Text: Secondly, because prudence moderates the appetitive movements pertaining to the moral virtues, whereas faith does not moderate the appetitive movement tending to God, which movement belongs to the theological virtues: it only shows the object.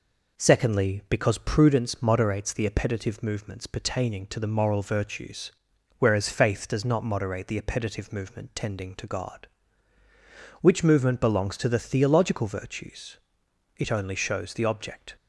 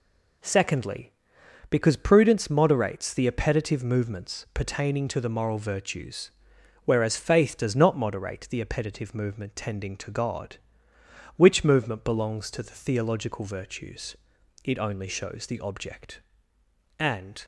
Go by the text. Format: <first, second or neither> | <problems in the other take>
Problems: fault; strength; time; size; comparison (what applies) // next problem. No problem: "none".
first | goes on to say "And"; slight; from 16.9 s on; 0.46 s long